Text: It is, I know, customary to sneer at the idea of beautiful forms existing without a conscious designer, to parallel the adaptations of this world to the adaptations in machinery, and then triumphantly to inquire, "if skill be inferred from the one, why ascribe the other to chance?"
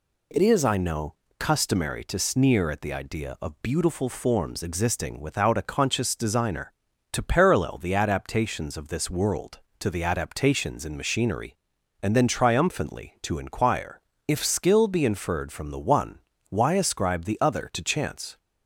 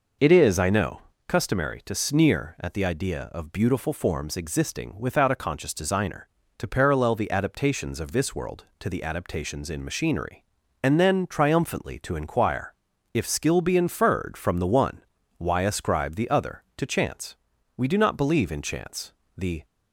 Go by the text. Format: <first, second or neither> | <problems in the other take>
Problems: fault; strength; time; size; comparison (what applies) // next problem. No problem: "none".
first | goes on to say "We do not believe in chance the"; strong; from 17.7 s on; 1.8 s long